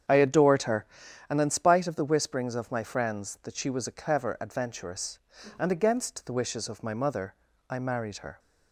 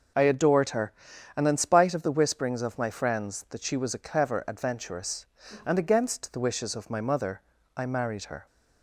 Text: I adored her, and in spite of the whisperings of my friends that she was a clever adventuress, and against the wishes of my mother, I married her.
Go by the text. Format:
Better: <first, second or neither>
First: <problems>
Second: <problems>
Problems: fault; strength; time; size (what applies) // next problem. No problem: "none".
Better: second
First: starts louder than the rest; strong; until 1.1 s; 8 dB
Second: none